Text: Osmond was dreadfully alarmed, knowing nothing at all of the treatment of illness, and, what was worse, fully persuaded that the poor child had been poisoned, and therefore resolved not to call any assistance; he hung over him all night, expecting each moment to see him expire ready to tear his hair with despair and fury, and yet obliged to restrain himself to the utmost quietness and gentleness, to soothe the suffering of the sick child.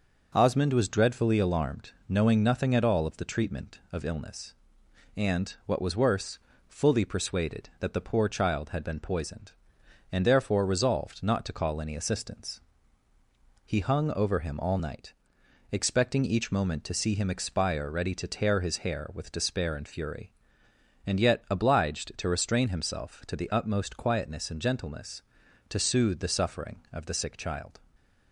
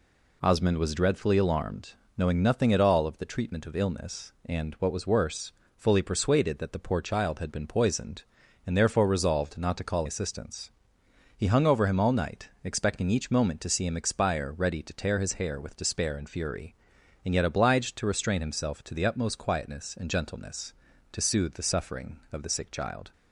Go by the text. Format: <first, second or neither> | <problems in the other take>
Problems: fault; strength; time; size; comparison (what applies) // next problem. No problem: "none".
first | skips "any"; at 10.0 s